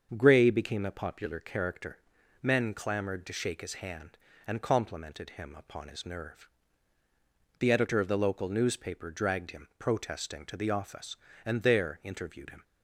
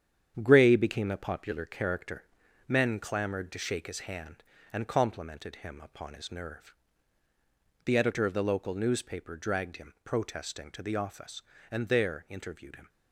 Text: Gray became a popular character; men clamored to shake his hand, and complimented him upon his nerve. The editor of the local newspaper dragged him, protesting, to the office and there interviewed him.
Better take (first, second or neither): first